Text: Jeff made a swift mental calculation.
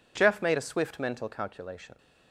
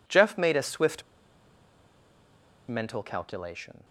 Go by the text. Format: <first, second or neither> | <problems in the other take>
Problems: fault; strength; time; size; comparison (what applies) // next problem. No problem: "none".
first | pauses between "swift" and "mental"; strong; at 1.0 s; 1.6 s long